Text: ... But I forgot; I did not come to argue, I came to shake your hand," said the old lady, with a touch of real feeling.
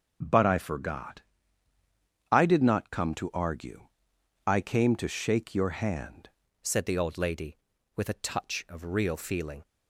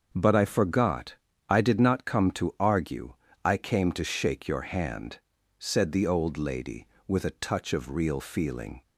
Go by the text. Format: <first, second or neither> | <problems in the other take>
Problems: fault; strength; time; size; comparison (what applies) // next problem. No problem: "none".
second | starts louder than the rest; noticeable; until 1.2 s; 6 dB; also in the second // changes voice at "said"; from 6.6 s on; 3.0 s long